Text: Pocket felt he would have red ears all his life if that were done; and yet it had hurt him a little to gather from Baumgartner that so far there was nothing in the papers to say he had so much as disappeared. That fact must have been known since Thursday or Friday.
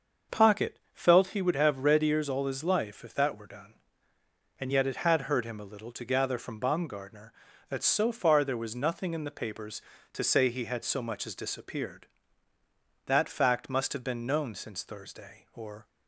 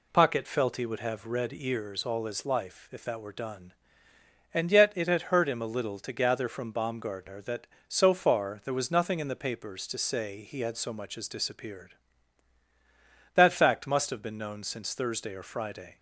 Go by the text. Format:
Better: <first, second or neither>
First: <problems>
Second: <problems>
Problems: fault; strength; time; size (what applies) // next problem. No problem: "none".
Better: second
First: starts louder than the rest; until 1.4 s; 6.5 dB // stops before "Friday"; at 15.8 s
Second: none